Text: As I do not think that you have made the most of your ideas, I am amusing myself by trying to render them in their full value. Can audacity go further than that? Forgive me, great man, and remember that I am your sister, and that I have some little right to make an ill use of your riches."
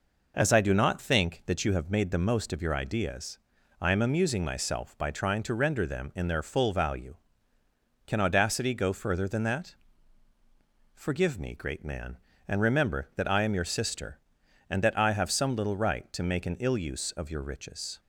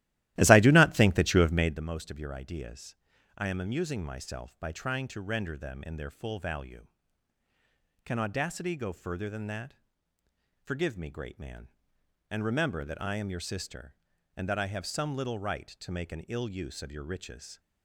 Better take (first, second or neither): first